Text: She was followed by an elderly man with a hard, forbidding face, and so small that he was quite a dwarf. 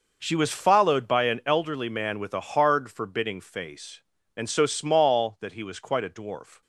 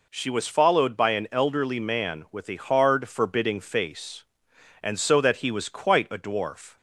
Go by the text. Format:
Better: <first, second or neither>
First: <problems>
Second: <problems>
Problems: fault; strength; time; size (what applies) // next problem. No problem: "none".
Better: first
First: none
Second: skips "small"; at 5.2 s